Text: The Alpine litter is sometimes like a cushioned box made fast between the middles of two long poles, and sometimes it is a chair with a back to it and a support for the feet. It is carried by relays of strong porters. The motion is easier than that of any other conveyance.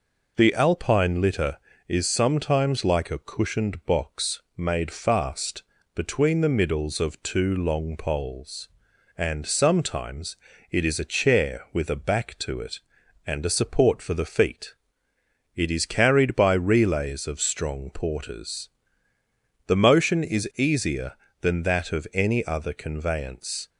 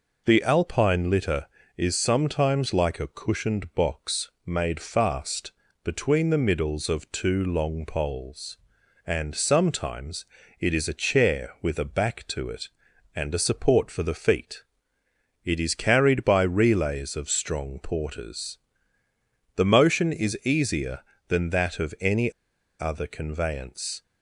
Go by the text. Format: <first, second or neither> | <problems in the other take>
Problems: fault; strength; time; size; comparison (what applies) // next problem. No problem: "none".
first | pauses between "box" and "made"; slight; at 4.2 s; 0.16 s long; slight in the first // pauses between "fast" and "between"; slight; at 5.4 s; 0.32 s long; slight in the first // pauses between "sometimes" and "it"; slight; at 10.2 s; 0.36 s long; slight in the first // pauses between "any" and "other"; noticeable; at 22.3 s; 0.47 s long